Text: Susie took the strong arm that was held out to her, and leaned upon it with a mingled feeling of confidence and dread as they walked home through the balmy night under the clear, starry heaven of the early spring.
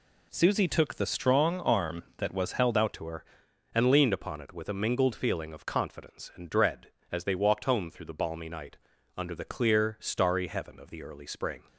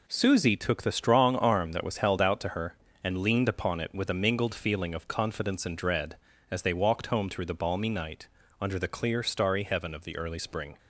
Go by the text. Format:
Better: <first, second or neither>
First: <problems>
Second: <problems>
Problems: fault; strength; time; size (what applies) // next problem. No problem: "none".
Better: second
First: changes voice at "to"; from 2.9 s on; 8.7 s long // pauses between "night" and "under"; at 8.7 s; 0.40 s long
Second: pauses between "night" and "under"; slight; at 8.2 s; 0.32 s long